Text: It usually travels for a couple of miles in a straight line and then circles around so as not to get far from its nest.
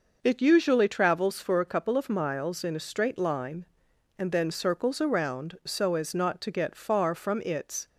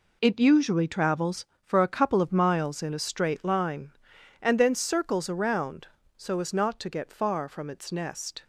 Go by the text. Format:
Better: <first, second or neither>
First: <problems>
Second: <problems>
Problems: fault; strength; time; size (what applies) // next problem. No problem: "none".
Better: second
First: stops before "nest"; at 7.8 s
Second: none